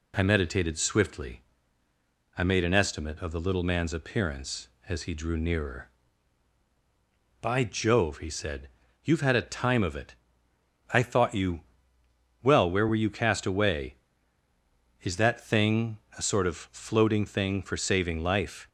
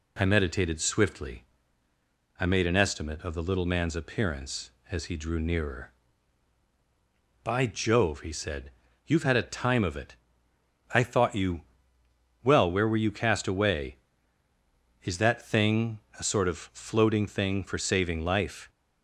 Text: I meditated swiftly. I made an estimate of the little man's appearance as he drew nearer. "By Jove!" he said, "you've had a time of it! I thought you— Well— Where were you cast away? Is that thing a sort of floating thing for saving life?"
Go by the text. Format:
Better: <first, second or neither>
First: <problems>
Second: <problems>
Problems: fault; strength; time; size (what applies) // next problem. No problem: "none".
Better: neither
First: pauses between "thing" and "a"; slight; at 15.9 s; 0.18 s long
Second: pauses between "thing" and "a"; slight; at 15.9 s; 0.18 s long